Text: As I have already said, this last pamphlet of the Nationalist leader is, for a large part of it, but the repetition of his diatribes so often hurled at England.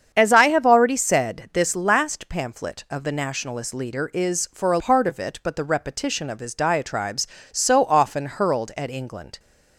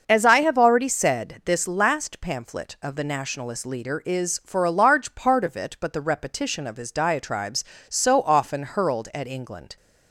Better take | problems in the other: second | starts louder than the rest; strong; until 1.1 s; 7.5 dB; also in the second // skips "large"; at 4.7 s

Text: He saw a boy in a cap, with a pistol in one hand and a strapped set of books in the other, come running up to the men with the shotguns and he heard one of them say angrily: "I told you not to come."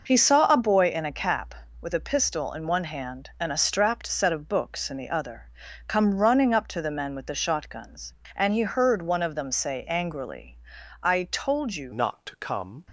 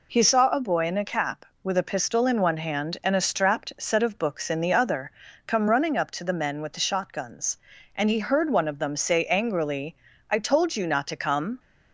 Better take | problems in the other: second | changes voice at "not"; from 11.9 s on; 0.9 s long

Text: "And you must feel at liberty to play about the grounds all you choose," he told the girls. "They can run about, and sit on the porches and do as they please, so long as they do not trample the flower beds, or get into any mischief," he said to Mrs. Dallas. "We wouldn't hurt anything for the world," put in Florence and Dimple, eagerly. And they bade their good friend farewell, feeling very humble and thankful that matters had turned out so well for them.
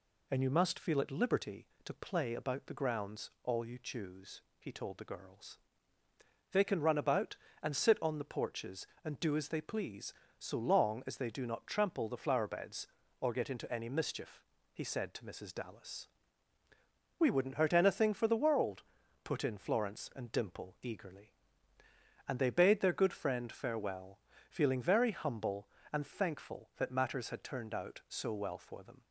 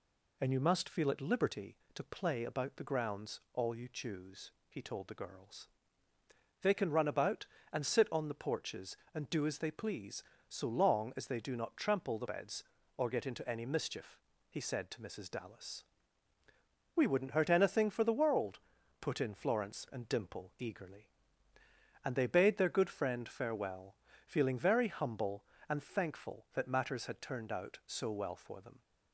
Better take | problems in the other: first | skips "flower"; at 12.2 s

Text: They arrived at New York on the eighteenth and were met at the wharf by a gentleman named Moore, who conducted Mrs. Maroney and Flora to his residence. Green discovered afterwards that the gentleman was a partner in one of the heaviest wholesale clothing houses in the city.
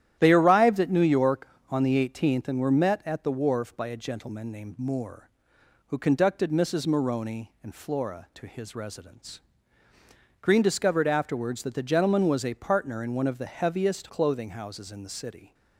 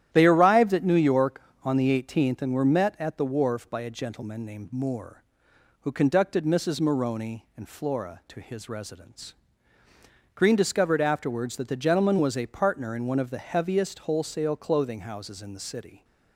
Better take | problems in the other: second | starts louder than the rest; strong; until 1.2 s; 11.5 dB; strong in the second // skips "wholesale"; at 14.0 s

